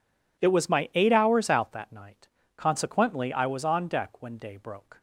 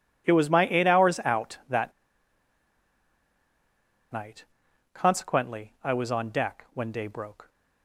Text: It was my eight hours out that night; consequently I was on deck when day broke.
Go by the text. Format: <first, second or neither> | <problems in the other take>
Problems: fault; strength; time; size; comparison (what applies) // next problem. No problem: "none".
first | pauses between "that" and "night"; strong; at 1.9 s; 2.1 s long